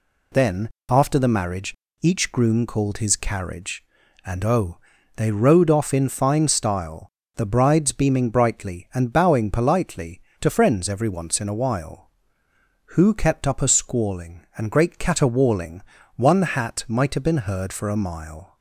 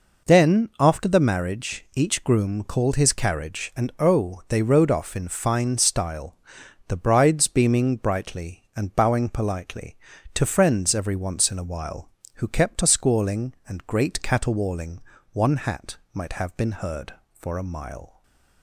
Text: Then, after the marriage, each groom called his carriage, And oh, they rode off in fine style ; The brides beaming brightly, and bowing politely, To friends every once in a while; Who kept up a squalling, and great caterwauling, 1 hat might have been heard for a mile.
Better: first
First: none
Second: skips "up"; at 12.8 s // pauses between "hat" and "might"; slight; at 15.9 s; 0.16 s long // stays silent after the last word; slight; from 18.0 s on; 0.6 s long

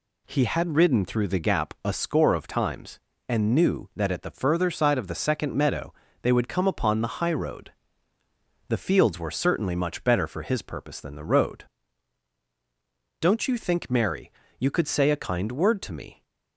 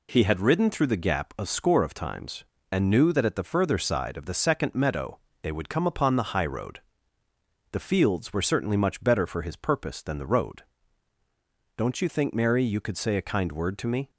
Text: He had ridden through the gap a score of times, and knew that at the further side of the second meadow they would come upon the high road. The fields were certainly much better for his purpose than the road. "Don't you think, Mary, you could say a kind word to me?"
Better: neither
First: pauses between "meadow" and "they"; slight; at 5.9 s; 0.30 s long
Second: pauses between "meadow" and "they"; slight; at 5.1 s; 0.24 s long

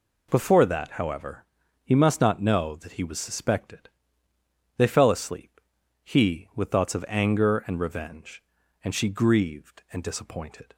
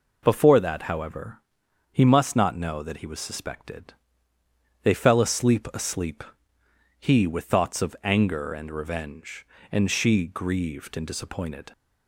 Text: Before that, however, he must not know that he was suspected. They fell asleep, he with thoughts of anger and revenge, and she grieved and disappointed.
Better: first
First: none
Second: says "asleep" twice; at 5.7 s

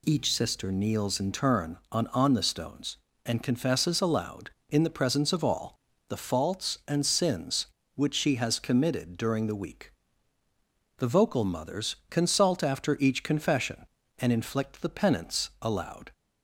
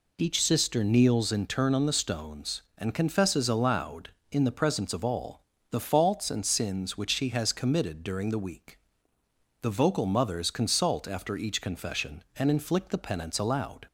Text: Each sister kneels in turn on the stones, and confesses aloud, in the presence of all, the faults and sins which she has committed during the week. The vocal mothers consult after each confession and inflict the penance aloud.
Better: second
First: says "on" twice; at 2.0 s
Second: none

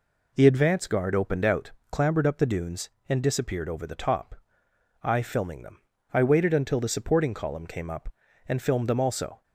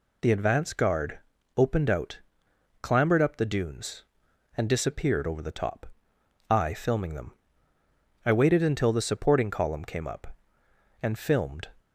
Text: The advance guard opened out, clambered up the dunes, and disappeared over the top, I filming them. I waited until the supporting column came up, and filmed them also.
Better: first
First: none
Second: pauses between "guard" and "opened"; slight; at 1.1 s; 0.36 s long // stops before "them also"; at 11.7 s

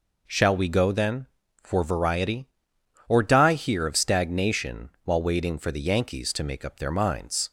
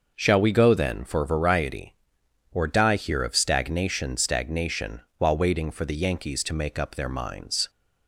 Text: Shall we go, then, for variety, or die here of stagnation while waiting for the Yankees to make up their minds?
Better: first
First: none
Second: says "stagnation" twice; at 4.1 s

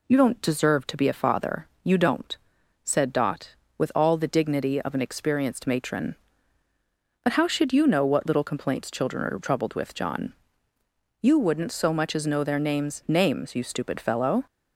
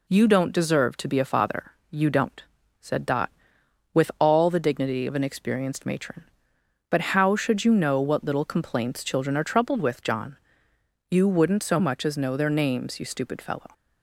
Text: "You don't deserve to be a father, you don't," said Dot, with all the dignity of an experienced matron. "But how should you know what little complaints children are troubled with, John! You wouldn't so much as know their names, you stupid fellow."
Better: second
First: says "names" twice; at 13.0 s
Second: none

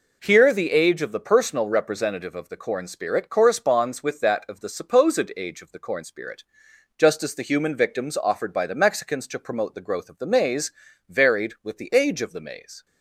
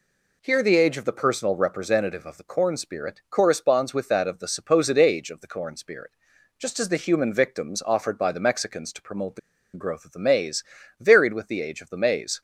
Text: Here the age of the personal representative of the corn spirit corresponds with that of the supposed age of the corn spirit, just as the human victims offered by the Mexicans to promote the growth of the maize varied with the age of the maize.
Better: first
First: pauses between "maize" and "varied"; at 10.7 s; 0.38 s long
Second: pauses between "the" and "growth"; slight; at 9.3 s; 0.35 s long // pauses between "maize" and "varied"; slight; at 10.6 s; 0.36 s long

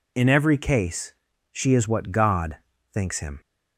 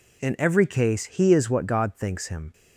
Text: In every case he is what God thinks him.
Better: second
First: says "she" for "he"; at 1.5 s // pauses between "God" and "thinks"; at 2.5 s; 0.38 s long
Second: none

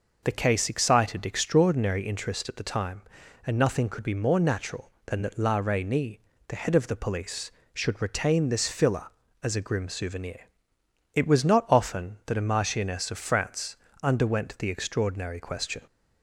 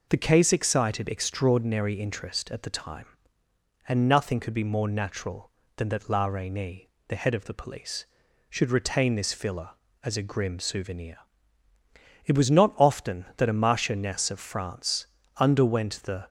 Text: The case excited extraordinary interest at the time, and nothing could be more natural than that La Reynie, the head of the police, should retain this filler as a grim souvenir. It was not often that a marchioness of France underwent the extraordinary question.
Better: first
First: pauses between "France" and "underwent"; slight; at 13.7 s; 0.26 s long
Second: pauses between "France" and "underwent"; slight; at 15.0 s; 0.30 s long // stops before "extraordinary question"; at 16.2 s

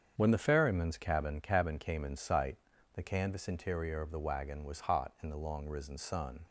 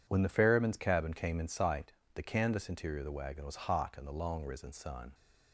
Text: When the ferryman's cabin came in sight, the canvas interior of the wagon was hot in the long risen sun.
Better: second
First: starts louder than the rest; strong; until 1.1 s; 7.5 dB // says "cabin" twice; at 1.4 s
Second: none

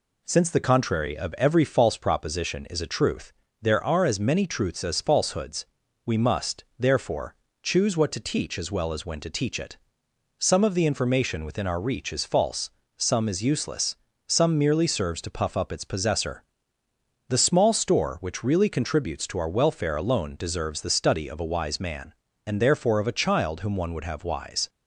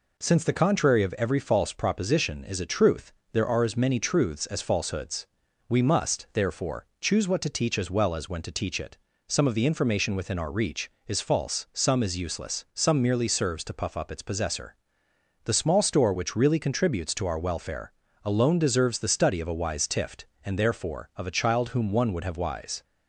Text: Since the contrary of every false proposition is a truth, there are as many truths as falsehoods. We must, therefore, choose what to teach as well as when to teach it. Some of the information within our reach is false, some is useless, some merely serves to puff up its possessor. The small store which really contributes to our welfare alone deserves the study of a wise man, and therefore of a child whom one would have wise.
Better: first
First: none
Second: pauses between "welfare" and "alone"; slight; at 17.9 s; 0.34 s long // says "tift" for "man"; at 19.8 s

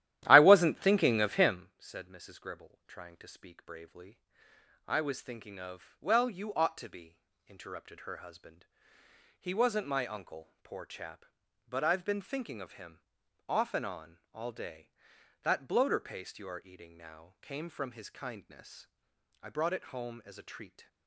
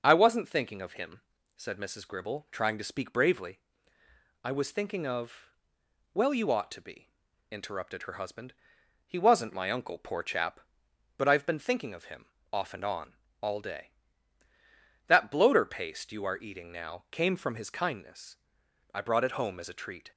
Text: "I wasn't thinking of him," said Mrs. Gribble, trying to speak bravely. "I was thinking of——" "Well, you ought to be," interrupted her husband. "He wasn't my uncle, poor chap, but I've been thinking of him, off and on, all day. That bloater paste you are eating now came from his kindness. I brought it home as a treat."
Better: second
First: starts louder than the rest; strong; until 1.6 s; 13 dB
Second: none

